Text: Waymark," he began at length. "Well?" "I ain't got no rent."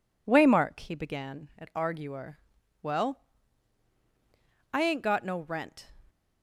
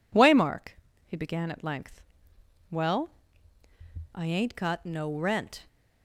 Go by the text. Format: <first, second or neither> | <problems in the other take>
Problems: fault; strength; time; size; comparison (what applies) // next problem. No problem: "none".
second | says "arguer" for "length"; at 1.7 s